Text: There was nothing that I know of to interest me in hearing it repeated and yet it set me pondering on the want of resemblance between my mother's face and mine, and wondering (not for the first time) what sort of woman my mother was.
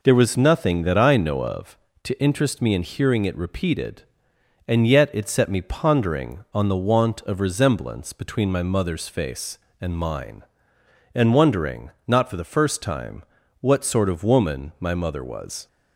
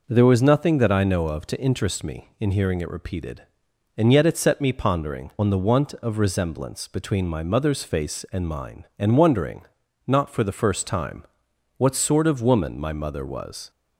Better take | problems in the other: neither | none

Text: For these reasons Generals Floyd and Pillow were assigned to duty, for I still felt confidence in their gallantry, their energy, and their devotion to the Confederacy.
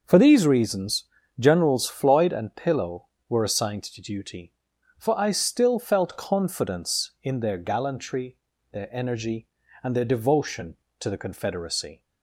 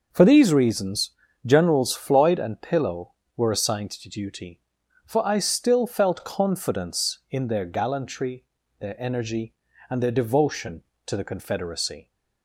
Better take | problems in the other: neither | pauses between "reasons" and "Generals"; slight; the same in both

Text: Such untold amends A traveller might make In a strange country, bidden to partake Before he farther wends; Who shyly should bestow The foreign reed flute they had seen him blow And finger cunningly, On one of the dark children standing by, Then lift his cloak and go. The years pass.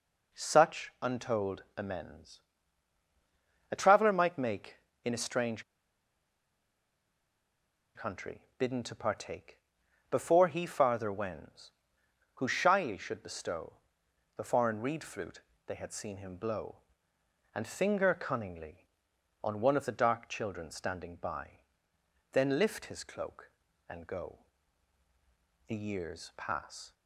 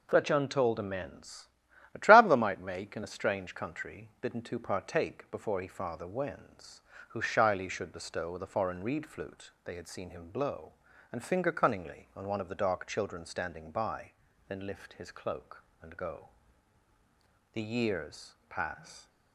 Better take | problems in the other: second | pauses between "amends" and "A"; strong; at 2.4 s; 1.3 s long; also in the second // pauses between "strange" and "country"; strong; at 5.6 s; 2.3 s long // pauses between "partake" and "Before"; noticeable; at 9.5 s; 0.52 s long // pauses between "bestow" and "The"; noticeable; at 13.7 s; 0.64 s long // pauses between "flute" and "they"; slight; at 15.4 s; 0.24 s long; slight in the second

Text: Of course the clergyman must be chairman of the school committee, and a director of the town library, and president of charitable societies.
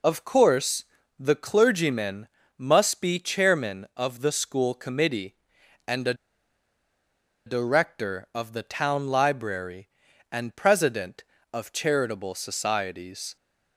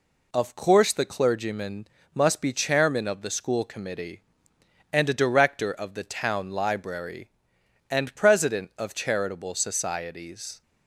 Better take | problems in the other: second | pauses between "course" and "the"; slight; at 0.8 s; 0.34 s long // pauses between "clergyman" and "must"; slight; at 2.2 s; 0.28 s long; slight in the second // pauses between "a" and "director"; strong; at 6.1 s; 1.3 s long

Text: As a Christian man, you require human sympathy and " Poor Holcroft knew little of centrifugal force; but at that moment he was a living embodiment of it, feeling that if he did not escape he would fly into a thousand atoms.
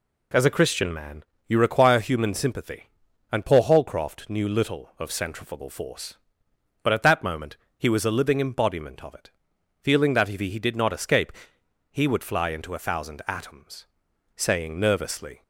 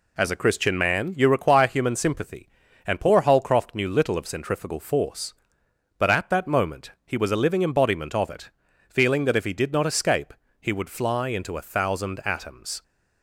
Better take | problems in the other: second | pauses between "moment" and "he"; slight; at 7.5 s; 0.18 s long; slight in the second // pauses between "escape" and "he"; noticeable; at 11.3 s; 0.58 s long; slight in the second // goes on to say "Saying nervously"; noticeable; from 14.3 s on; 1.0 s long

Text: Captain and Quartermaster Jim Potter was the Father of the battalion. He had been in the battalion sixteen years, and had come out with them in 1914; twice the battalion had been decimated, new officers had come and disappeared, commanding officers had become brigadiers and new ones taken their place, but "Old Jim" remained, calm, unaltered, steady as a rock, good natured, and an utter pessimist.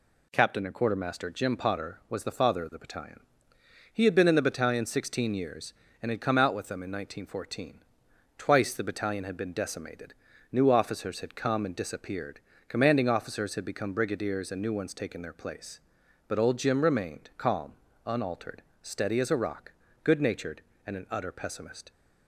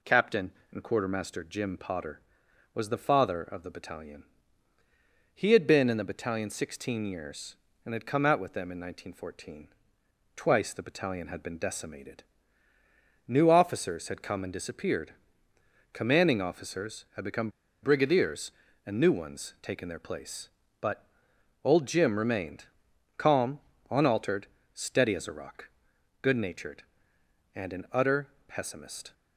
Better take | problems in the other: first | pauses between "become" and "brigadiers"; slight; at 17.4 s; 0.32 s long // pauses between "but" and "Old"; noticeable; at 21.0 s; 0.58 s long // pauses between "utter" and "pessimist"; slight; at 28.2 s; 0.18 s long

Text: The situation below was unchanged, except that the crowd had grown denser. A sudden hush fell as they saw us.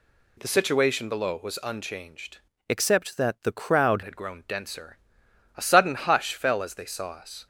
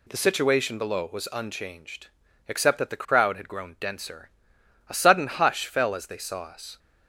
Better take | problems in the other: second | changes voice from "except" to "crowd"; from 2.6 to 4.0 s; 1.4 s long

